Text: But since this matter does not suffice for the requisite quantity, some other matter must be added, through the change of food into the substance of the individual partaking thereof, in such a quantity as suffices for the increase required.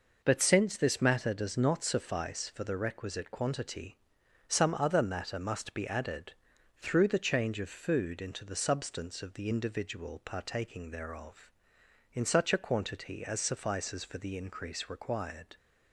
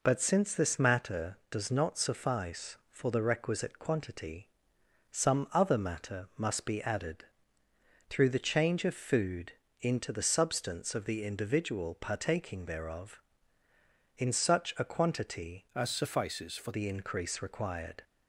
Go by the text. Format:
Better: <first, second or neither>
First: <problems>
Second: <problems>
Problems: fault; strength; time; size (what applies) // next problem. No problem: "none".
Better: first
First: none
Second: pauses between "food" and "into"; slight; at 9.5 s; 0.28 s long // changes voice from "as" to "for"; from 15.7 to 16.7 s; 1.0 s long